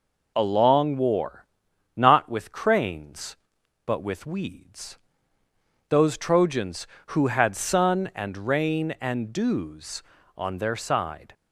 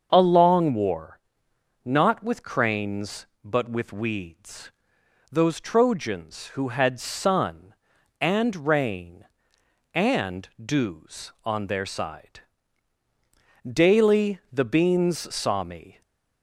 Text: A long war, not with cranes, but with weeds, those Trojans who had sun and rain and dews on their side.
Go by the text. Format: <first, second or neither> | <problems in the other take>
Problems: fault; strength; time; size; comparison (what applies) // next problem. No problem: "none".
first | starts louder than the rest; until 1.1 s; 6.5 dB // goes on to say "Daily the beans saw me"; strong; from 13.6 s on; 2.3 s long // stays silent after the last word; slight; from 15.9 s on; 0.5 s long